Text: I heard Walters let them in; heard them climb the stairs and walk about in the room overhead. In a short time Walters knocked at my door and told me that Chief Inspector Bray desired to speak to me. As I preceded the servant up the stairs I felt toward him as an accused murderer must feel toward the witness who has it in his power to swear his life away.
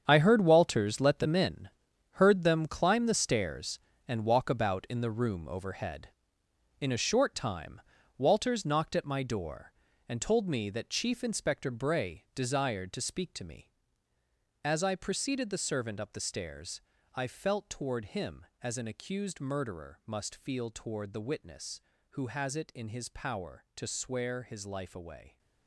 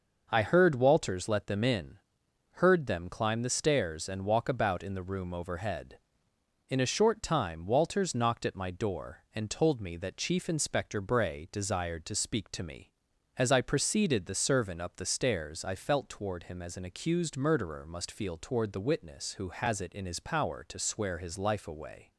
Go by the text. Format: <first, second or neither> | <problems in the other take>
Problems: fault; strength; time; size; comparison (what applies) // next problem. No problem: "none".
second | gets quieter; strong; throughout; 12 dB // pauses between "time" and "Walters"; at 7.8 s; 0.38 s long // pauses between "stairs" and "I"; slight; at 16.8 s; 0.34 s long